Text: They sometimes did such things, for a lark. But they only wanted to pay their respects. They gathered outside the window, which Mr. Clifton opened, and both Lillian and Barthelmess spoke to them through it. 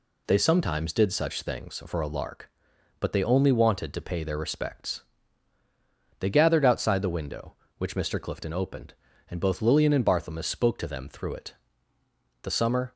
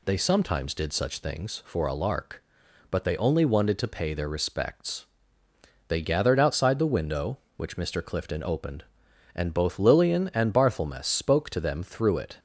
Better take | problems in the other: second | goes on to say "The summer"; from 12.4 s on; 0.50 s long

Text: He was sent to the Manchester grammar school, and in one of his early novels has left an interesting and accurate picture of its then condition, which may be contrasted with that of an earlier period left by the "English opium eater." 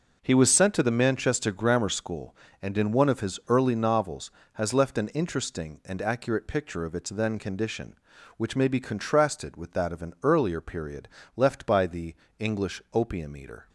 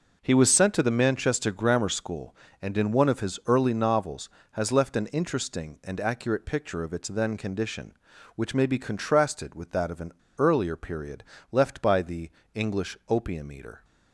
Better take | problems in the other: first | pauses between "an" and "earlier"; slight; at 10.1 s; 0.25 s long // pauses between "period" and "left"; slight; at 11.2 s; 0.30 s long; slight in the first // pauses between "the" and "English"; slight; at 12.2 s; 0.22 s long; slight in the first

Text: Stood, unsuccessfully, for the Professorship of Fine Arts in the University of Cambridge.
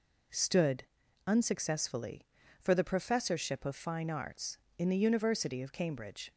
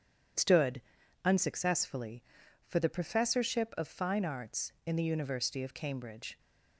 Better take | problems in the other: neither | none

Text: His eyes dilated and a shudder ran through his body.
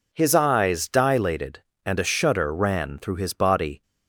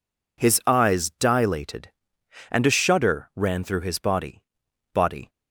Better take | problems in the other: first | says "body" twice; at 4.9 s

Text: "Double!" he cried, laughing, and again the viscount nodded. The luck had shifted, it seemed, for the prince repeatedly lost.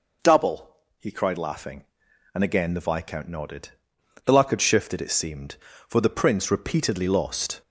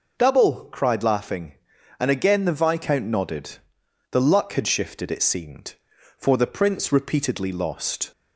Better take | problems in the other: first | skips "he"; at 0.6 s

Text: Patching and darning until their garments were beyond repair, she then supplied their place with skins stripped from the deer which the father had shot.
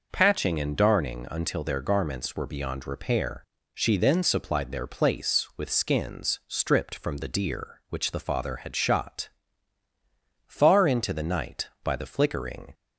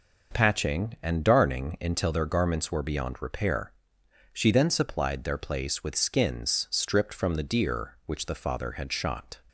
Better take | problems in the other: second | goes on to say "Far into the night by the flickering"; strong; from 10.4 s on; 2.2 s long

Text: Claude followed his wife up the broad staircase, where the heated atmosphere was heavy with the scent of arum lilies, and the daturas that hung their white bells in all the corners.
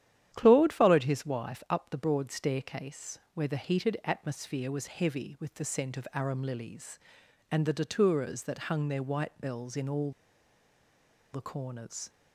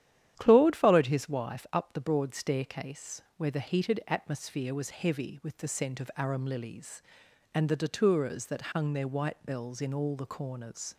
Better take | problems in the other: second | starts louder than the rest; strong; until 1.3 s; 10.5 dB; strong in the second // pauses between "all" and "the"; at 10.1 s; 1.2 s long

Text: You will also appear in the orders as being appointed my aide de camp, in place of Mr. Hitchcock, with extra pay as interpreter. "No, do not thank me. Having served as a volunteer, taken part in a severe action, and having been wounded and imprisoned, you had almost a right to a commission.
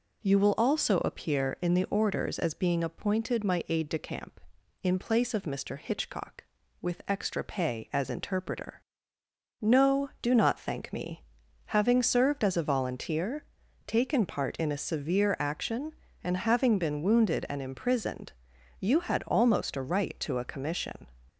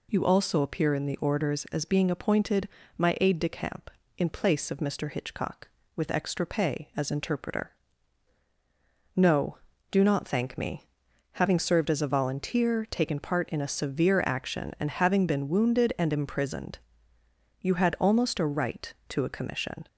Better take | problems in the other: first | skips "will"; at 0.2 s // pauses between "appointed" and "my"; slight; at 2.6 s; 0.30 s long

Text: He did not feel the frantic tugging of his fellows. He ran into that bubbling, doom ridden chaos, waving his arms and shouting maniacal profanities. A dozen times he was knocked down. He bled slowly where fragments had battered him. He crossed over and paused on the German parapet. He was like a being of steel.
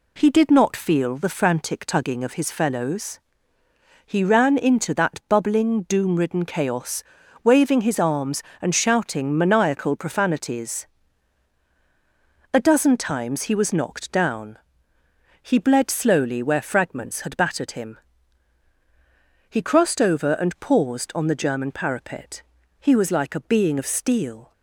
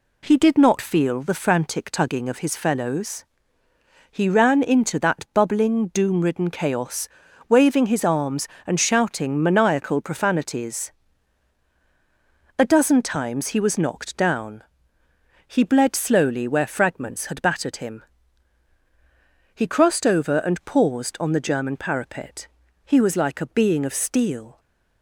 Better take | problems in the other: neither | none

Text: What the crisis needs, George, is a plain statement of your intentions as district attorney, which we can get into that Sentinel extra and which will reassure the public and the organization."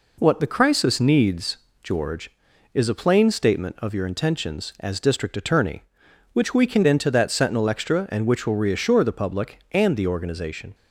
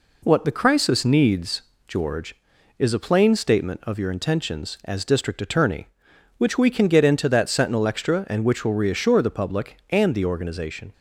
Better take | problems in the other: second | skips "get"; at 6.8 s

